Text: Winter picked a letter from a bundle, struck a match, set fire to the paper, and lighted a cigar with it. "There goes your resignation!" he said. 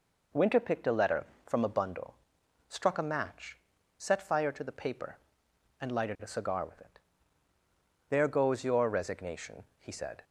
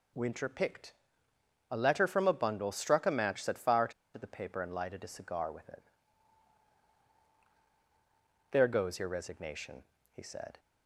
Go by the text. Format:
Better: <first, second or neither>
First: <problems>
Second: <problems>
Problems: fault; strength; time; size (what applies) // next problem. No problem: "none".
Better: first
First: none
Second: pauses between "picked" and "a"; noticeable; at 0.9 s; 0.78 s long // pauses between "to" and "the"; slight; at 3.9 s; 0.24 s long